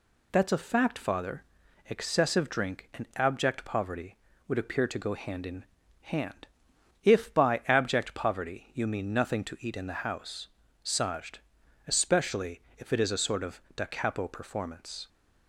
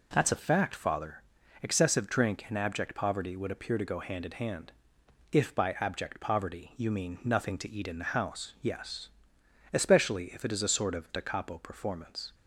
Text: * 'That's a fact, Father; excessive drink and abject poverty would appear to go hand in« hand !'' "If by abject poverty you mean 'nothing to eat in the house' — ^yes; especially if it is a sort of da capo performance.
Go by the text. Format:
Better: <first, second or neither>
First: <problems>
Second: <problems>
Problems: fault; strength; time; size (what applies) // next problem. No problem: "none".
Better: second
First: pauses between "in" and "hand"; at 5.6 s; 0.38 s long // says "sajd" for "yes"; at 10.8 s // pauses between "especially" and "if"; slight; at 12.6 s; 0.18 s long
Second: none